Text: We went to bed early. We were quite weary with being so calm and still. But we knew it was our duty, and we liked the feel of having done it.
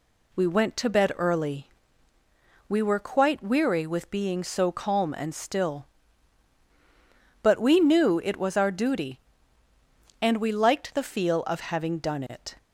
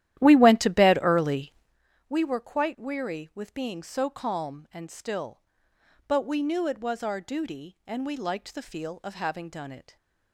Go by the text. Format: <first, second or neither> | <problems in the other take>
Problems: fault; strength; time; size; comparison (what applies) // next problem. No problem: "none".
first | starts louder than the rest; strong; until 1.8 s; 13 dB